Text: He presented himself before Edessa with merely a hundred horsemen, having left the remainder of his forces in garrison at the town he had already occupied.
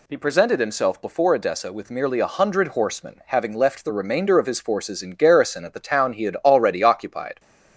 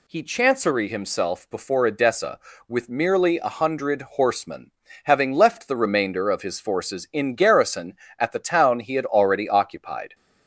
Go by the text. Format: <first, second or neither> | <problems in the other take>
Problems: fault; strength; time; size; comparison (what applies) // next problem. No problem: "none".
first | says "chancery" for "presented"; at 0.2 s